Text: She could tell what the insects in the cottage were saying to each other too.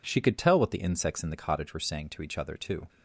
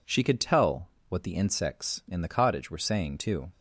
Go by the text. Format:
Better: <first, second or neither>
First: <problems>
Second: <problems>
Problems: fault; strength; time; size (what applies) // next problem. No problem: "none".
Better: first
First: none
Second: pauses between "tell" and "what"; slight; at 0.8 s; 0.22 s long // skips "to each other"; at 3.1 s